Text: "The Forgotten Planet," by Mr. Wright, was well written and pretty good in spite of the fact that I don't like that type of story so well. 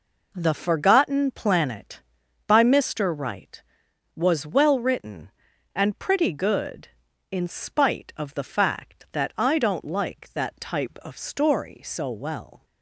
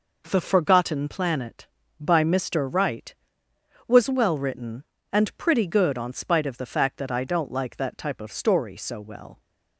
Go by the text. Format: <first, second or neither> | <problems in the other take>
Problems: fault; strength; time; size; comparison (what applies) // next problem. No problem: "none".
first | says "on" for "in"; at 5.9 s